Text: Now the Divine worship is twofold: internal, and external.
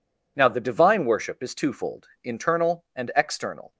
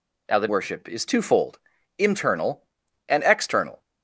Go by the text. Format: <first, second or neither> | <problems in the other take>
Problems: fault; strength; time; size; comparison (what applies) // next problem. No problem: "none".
first | skips "Divine"; at 0.4 s